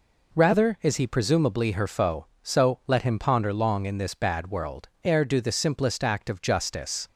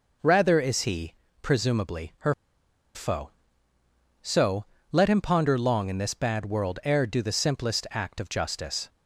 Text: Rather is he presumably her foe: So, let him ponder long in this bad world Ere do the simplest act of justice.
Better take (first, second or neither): first